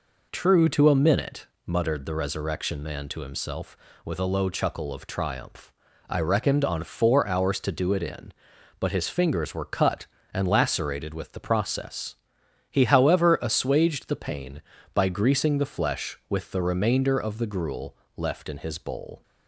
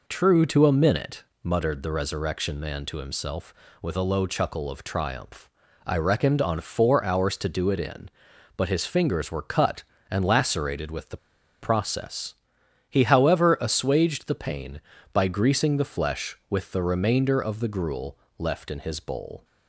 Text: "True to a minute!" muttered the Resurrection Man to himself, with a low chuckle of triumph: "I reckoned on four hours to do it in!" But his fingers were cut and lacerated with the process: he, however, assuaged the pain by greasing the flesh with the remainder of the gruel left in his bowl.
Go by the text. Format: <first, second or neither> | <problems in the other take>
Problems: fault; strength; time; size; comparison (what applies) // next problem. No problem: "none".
first | pauses between "the" and "process"; at 11.1 s; 0.45 s long // pauses between "gruel" and "left"; slight; at 18.1 s; 0.20 s long; slight in the first